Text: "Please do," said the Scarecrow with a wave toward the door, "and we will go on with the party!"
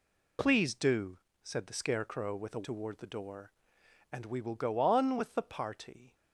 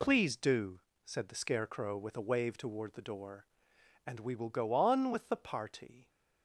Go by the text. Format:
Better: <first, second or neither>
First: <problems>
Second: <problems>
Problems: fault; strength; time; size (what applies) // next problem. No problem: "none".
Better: second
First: skips "wave"; at 2.6 s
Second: none